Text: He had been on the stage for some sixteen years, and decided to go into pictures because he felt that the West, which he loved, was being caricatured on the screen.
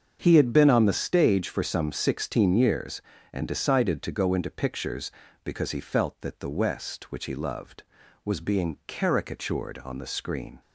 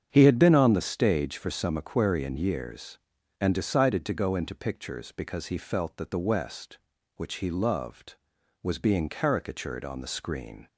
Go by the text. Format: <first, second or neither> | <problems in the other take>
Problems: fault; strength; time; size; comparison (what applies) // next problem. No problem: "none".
first | starts louder than the rest; strong; until 1.1 s; 8 dB; also in the first // says "aquarian" for "sixteen"; at 1.7 s